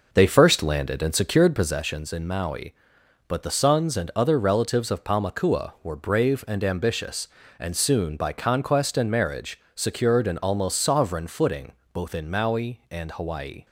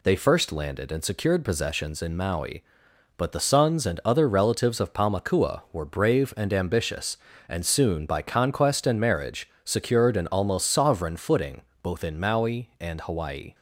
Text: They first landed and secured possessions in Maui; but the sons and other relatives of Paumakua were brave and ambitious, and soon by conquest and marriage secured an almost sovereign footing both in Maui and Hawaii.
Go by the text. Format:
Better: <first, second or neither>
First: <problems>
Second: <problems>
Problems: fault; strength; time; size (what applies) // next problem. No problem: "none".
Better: second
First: starts louder than the rest; noticeable; until 1.7 s; 5 dB // pauses between "footing" and "both"; slight; at 11.7 s; 0.20 s long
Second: pauses between "footing" and "both"; slight; at 11.6 s; 0.20 s long